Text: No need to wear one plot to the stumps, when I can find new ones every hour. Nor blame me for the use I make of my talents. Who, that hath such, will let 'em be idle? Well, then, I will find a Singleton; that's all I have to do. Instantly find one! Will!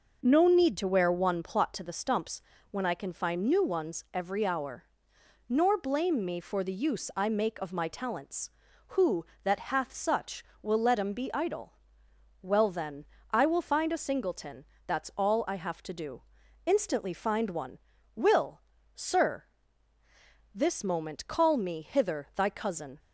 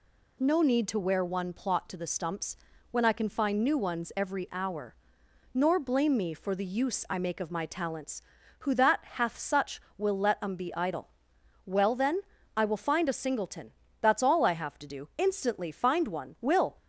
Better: second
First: goes on to say "Sir This moment call me hither thy cousin"; strong; from 18.9 s on; 4.0 s long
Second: none

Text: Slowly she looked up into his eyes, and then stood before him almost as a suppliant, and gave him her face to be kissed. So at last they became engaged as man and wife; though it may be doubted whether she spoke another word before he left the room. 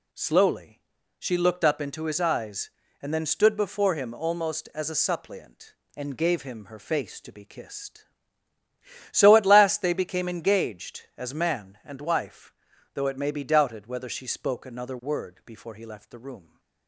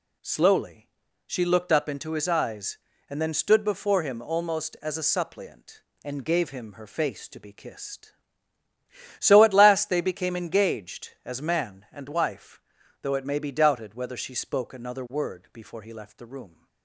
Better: neither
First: pauses between "Slowly" and "she"; at 0.7 s; 0.40 s long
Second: pauses between "Slowly" and "she"; at 0.8 s; 0.40 s long

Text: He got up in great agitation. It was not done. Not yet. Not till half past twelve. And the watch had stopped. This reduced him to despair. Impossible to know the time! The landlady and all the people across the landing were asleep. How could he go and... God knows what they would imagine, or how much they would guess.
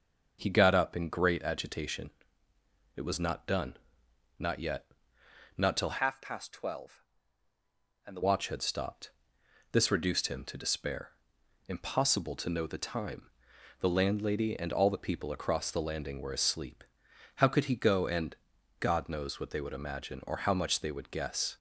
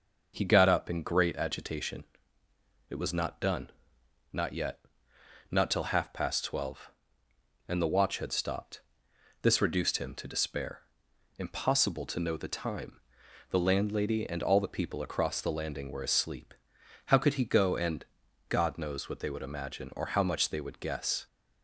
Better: second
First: starts louder than the rest; noticeable; until 1.4 s; 6 dB // changes voice from "half" to "the"; from 5.9 to 8.2 s; 2.3 s long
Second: none

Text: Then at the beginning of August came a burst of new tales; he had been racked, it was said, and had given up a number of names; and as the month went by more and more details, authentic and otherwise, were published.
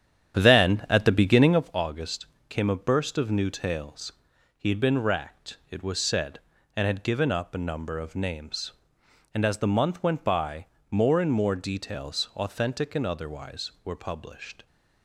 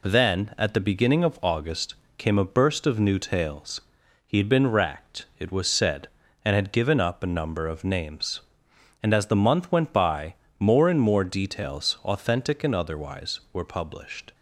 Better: second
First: starts louder than the rest; strong; until 1.7 s; 9.5 dB // pauses between "August" and "came"; slight; at 2.2 s; 0.24 s long // pauses between "by" and "more"; slight; at 10.6 s; 0.26 s long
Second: pauses between "August" and "came"; slight; at 1.9 s; 0.24 s long // pauses between "by" and "more"; slight; at 10.3 s; 0.26 s long

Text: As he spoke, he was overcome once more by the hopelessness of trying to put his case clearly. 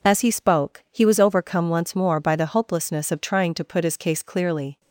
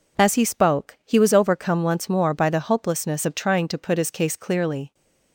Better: neither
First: none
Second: none

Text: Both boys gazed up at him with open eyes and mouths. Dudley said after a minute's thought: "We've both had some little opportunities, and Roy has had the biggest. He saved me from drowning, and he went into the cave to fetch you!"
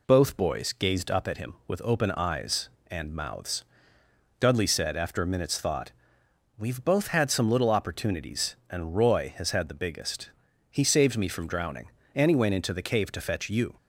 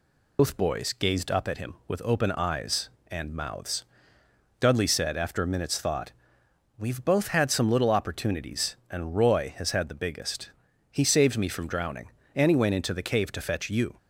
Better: first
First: none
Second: loses the start of "Both"; at 0.3 s; 125 ms

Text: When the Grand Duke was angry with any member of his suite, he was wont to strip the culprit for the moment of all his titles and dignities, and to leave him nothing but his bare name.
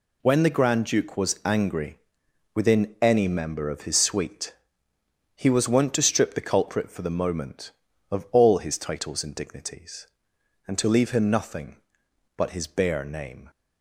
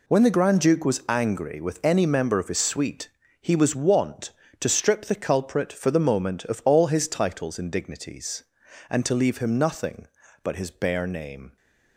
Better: second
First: says "within" for "with"; at 2.5 s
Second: none

